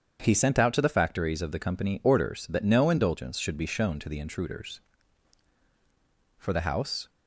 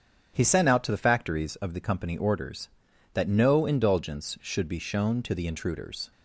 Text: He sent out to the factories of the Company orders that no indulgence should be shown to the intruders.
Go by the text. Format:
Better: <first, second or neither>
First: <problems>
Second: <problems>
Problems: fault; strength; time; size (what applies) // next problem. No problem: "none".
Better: second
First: starts louder than the rest; strong; until 1.2 s; 7.5 dB // goes on to say "For the House"; noticeable; from 6.3 s on; 0.72 s long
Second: starts louder than the rest; strong; until 1.3 s; 8 dB